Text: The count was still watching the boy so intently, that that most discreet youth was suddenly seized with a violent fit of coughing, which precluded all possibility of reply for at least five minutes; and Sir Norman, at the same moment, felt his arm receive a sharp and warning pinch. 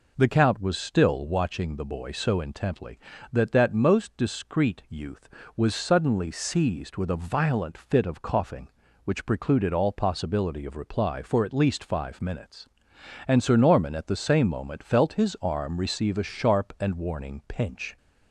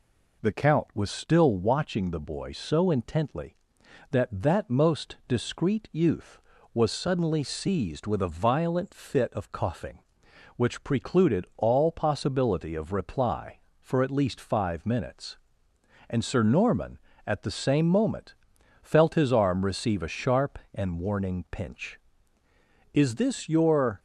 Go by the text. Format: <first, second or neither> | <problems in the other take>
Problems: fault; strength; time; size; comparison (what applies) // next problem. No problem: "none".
first | goes on to say "Is this your"; noticeable; from 22.9 s on; 1.0 s long